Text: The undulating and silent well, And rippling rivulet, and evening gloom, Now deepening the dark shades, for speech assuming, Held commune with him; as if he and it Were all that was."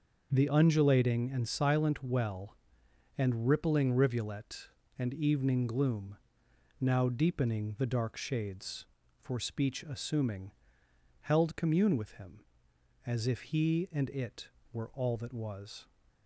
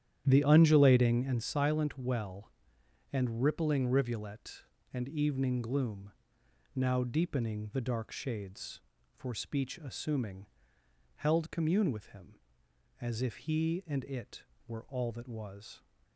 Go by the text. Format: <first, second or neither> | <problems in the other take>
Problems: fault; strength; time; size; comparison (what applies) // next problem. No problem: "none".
first | starts louder than the rest; strong; until 1.4 s; 10 dB